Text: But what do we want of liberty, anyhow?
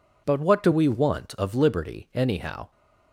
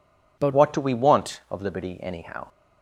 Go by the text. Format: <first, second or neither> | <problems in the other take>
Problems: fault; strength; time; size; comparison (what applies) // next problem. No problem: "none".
first | changes voice at "what"; from 0.5 s on; 1.9 s long